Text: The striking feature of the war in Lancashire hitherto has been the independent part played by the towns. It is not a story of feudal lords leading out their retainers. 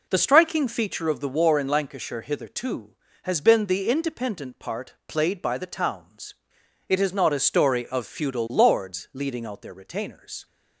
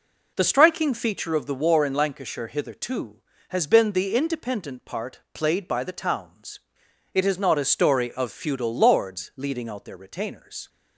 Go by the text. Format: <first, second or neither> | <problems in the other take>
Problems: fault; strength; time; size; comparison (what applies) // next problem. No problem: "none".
neither | none